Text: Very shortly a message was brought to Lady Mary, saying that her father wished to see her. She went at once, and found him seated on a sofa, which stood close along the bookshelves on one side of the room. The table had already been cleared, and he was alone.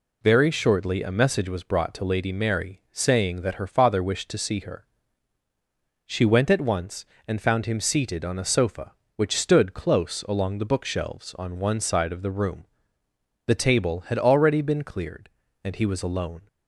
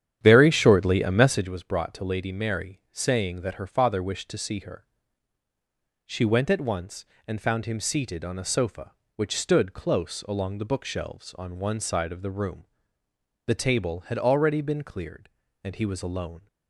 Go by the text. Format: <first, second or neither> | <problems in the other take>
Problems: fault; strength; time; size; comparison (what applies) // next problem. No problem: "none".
first | starts louder than the rest; strong; until 1.5 s; 9.5 dB